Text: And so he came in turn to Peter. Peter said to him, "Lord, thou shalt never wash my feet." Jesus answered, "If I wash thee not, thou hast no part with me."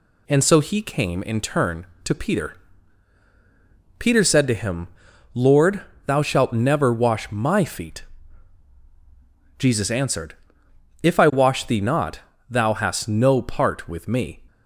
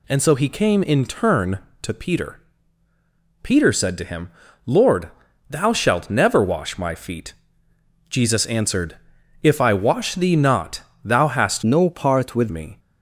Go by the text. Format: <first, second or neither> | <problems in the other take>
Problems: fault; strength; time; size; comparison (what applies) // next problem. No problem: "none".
first | changes voice from "no" to "with"; from 11.6 to 12.5 s; 0.9 s long